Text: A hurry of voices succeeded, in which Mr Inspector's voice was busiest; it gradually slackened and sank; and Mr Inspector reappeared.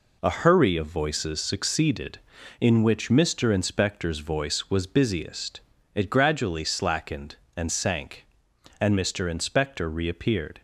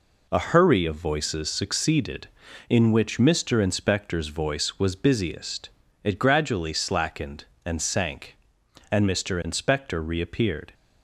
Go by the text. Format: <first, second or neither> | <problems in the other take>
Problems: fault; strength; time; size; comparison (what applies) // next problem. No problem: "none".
neither | none